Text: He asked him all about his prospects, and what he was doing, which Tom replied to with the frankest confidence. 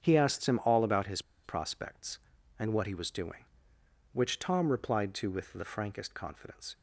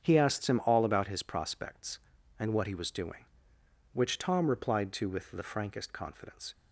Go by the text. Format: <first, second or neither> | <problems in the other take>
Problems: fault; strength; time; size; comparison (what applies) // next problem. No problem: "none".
second | starts louder than the rest; strong; until 1.0 s; 8 dB; strong in the second // pauses between "his" and "prospects"; slight; at 1.2 s; 0.23 s long